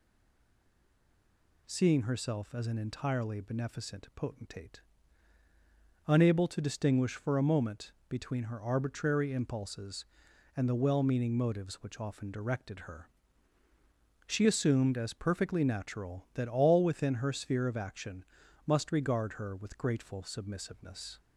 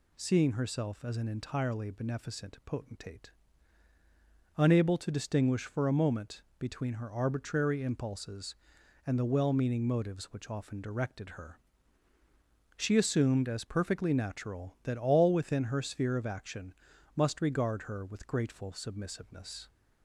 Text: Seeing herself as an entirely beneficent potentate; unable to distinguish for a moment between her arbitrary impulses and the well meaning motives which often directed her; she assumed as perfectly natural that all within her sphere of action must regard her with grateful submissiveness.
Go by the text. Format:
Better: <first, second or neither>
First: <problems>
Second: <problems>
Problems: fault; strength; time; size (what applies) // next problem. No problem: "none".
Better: second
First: stays silent before the first word; noticeable; until 1.6 s; 1.6 s long // pauses between "moment" and "between"; slight; at 7.9 s; 0.16 s long // pauses between "action" and "must"; at 18.2 s; 0.40 s long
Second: pauses between "moment" and "between"; slight; at 6.4 s; 0.16 s long // pauses between "action" and "must"; at 16.7 s; 0.40 s long